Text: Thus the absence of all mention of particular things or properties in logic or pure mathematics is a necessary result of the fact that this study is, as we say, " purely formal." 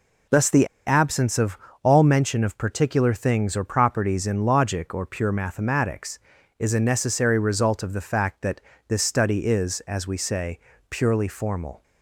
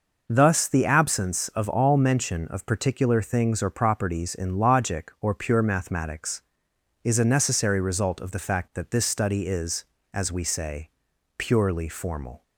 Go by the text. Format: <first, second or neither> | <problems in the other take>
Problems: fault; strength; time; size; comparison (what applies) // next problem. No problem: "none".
second | pauses between "the" and "absence"; slight; at 0.6 s; 0.20 s long // pauses between "of" and "all"; slight; at 1.5 s; 0.26 s long // pauses between "that" and "this"; slight; at 8.6 s; 0.26 s long